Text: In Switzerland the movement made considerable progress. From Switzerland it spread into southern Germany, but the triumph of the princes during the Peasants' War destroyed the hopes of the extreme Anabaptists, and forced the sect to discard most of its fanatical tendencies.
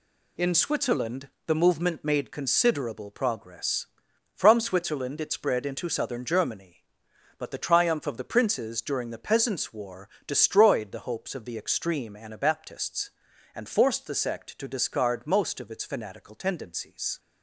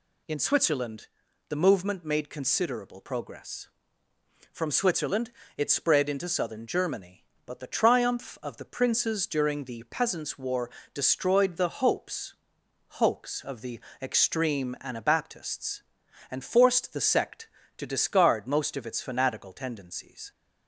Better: first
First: pauses between "Switzerland" and "the"; slight; at 1.2 s; 0.18 s long // pauses between "War" and "destroyed"; slight; at 10.0 s; 0.18 s long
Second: pauses between "Switzerland" and "the"; at 1.0 s; 0.40 s long // pauses between "Switzerland" and "it"; slight; at 5.3 s; 0.28 s long // pauses between "War" and "destroyed"; slight; at 10.7 s; 0.24 s long // says "hopes" twice; at 13.0 s // pauses between "the" and "extreme"; slight; at 13.8 s; 0.20 s long

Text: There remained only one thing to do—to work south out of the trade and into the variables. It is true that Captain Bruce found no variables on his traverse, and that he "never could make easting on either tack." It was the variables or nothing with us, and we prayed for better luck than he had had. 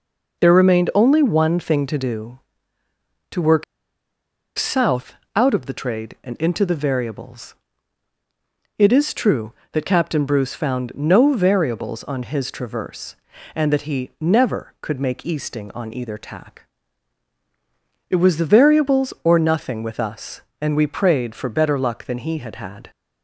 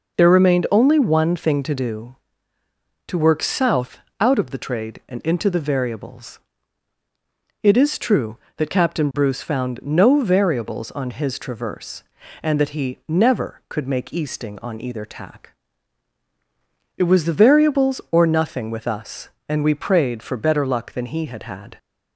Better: second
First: pauses between "work" and "south"; noticeable; at 3.6 s; 0.94 s long // pauses between "south" and "out"; slight; at 5.1 s; 0.22 s long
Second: pauses between "south" and "out"; slight; at 3.9 s; 0.22 s long

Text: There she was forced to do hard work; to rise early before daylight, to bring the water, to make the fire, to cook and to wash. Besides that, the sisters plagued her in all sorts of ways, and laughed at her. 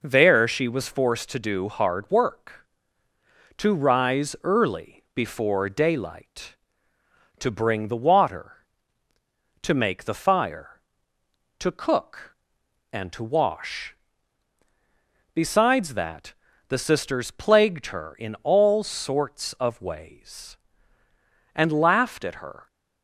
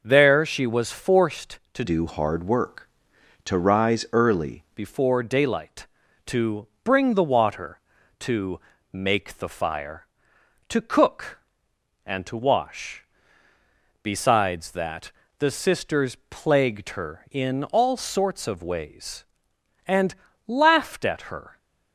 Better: first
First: none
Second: changes voice from "do" to "early"; from 1.8 to 4.6 s; 2.8 s long // pauses between "to" and "bring"; slight; at 6.6 s; 0.16 s long // pauses between "to" and "make"; slight; at 8.5 s; 0.32 s long // pauses between "and" and "laughed"; slight; at 20.1 s; 0.34 s long

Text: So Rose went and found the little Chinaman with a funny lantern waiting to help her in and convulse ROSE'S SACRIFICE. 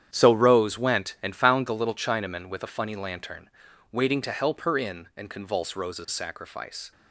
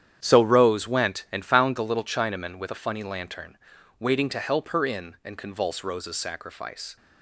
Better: neither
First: starts louder than the rest; strong; until 1.1 s; 9.5 dB // pauses between "lantern" and "waiting"; at 3.4 s; 0.44 s long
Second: starts louder than the rest; strong; until 1.2 s; 9.5 dB // pauses between "lantern" and "waiting"; at 3.5 s; 0.44 s long

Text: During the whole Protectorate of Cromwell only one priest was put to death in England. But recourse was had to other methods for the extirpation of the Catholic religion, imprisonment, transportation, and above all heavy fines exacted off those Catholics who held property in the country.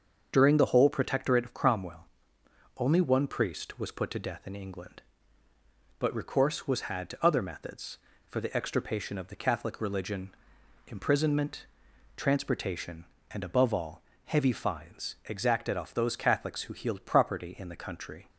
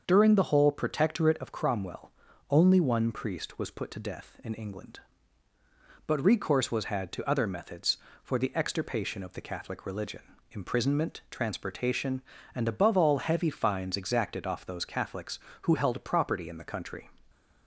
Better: second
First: starts louder than the rest; until 1.3 s; 7 dB // pauses between "Cromwell" and "only"; noticeable; at 2.0 s; 0.74 s long // pauses between "all" and "heavy"; slight; at 14.0 s; 0.24 s long // says "healed" for "held"; at 16.7 s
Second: starts louder than the rest; until 1.0 s; 6.5 dB // pauses between "Cromwell" and "only"; at 2.1 s; 0.40 s long

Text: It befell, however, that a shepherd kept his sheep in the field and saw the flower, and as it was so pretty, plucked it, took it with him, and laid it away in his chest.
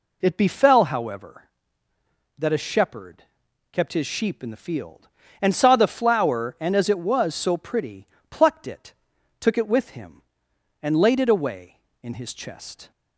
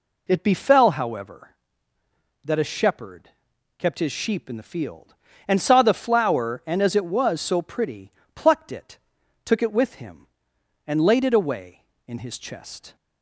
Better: neither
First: pauses between "shepherd" and "kept"; noticeable; at 3.2 s; 0.48 s long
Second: pauses between "shepherd" and "kept"; noticeable; at 3.2 s; 0.48 s long

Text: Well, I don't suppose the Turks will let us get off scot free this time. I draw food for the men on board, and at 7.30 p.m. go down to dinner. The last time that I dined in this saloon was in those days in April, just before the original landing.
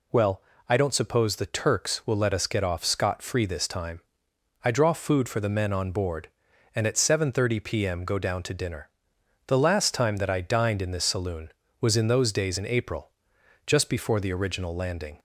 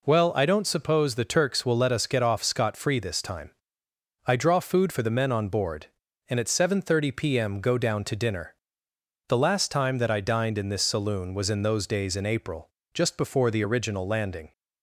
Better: neither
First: none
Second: none

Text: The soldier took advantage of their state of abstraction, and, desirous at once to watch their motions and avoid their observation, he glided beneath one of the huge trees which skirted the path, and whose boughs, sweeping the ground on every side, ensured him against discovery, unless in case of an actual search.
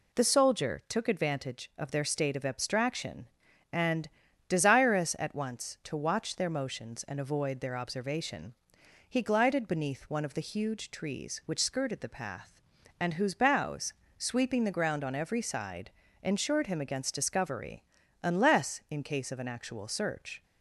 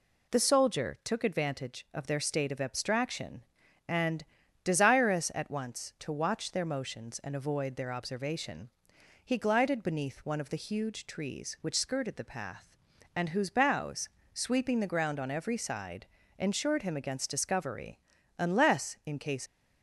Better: first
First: none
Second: stops before "of an actual search"; at 19.4 s

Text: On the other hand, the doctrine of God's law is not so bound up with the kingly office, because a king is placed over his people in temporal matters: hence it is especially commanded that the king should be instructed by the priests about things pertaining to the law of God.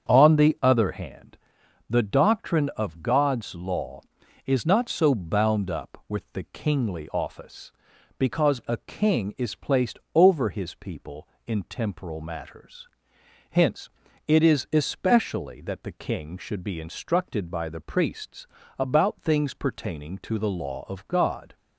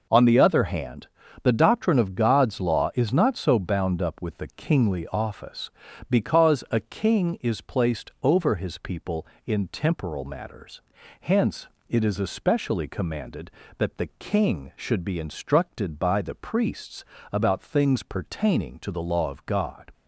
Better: second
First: starts louder than the rest; strong; until 1.1 s; 7.5 dB // pauses between "placed" and "over"; slight; at 9.9 s; 0.16 s long // pauses between "hence" and "it"; at 13.8 s; 0.38 s long // skips "commanded"; at 15.5 s // pauses between "priests" and "about"; slight; at 18.4 s; 0.32 s long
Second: pauses between "hence" and "it"; slight; at 11.6 s; 0.22 s long // pauses between "priests" and "about"; slight; at 17.0 s; 0.28 s long

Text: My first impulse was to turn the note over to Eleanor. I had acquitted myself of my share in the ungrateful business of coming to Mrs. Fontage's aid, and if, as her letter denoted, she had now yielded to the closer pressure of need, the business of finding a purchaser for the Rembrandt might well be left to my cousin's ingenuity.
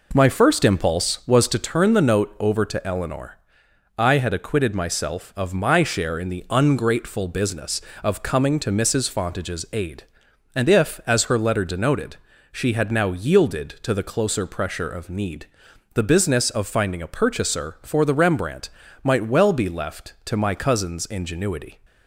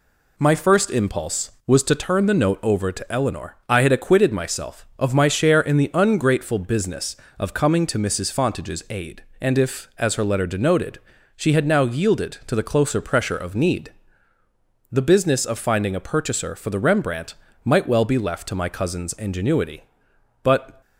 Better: first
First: pauses between "Rembrandt" and "might"; slight; at 18.6 s; 0.36 s long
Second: pauses between "Rembrandt" and "might"; slight; at 17.3 s; 0.30 s long // goes on to say "But"; slight; from 20.4 s on; 0.38 s long

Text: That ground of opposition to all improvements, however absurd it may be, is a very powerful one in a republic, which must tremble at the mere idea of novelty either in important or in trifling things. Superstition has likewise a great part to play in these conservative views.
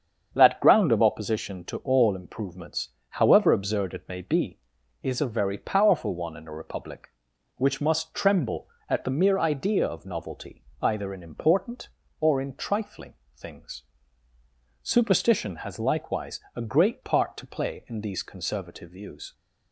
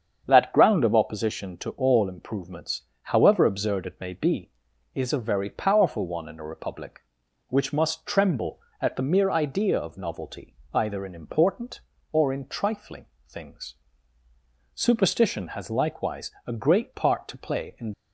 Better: first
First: starts louder than the rest; strong; until 1.3 s; 7.5 dB // pauses between "novelty" and "either"; slight; at 10.6 s; 0.18 s long // pauses between "trifling" and "things"; slight; at 13.1 s; 0.24 s long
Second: starts louder than the rest; strong; until 1.2 s; 7.5 dB // pauses between "novelty" and "either"; slight; at 10.5 s; 0.18 s long // pauses between "trifling" and "things"; slight; at 13.0 s; 0.24 s long // stops before "these conservative views"; at 17.9 s

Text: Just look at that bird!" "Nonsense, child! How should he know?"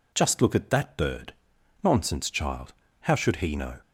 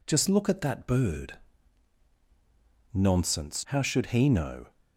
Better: first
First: none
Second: skips "child"; at 3.6 s

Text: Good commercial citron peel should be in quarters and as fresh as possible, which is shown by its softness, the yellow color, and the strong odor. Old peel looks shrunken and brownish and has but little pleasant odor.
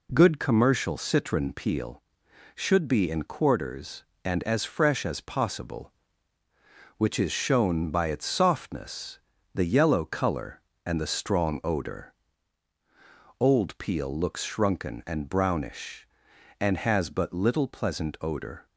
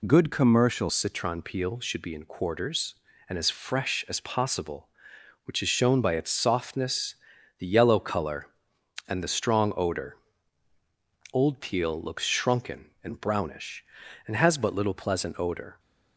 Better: first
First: none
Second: changes voice at "citron"; from 0.8 s on; 14.9 s long

